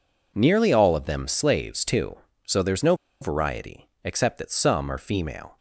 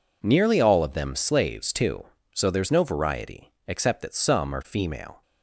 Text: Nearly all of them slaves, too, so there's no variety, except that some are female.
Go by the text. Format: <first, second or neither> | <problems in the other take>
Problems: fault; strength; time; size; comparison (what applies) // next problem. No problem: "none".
second | pauses between "no" and "variety"; slight; at 2.9 s; 0.26 s long